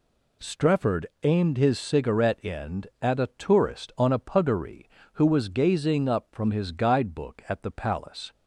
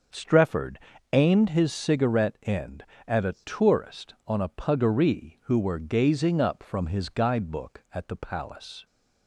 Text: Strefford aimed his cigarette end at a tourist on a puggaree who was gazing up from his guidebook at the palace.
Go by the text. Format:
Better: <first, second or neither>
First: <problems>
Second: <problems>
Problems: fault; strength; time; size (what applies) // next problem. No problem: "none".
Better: first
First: pauses between "Strefford" and "aimed"; slight; at 1.0 s; 0.18 s long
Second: starts louder than the rest; until 1.4 s; 6.5 dB // pauses between "Strefford" and "aimed"; slight; at 0.7 s; 0.36 s long // says "were" for "was"; at 5.5 s